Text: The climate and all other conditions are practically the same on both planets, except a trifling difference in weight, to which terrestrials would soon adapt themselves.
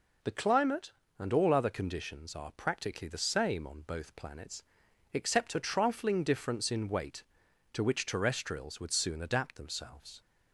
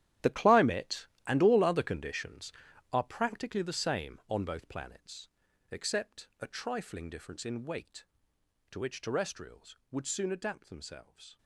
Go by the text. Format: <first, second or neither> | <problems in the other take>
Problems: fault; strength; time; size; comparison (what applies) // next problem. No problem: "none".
first | gets quieter; strong; throughout; 14 dB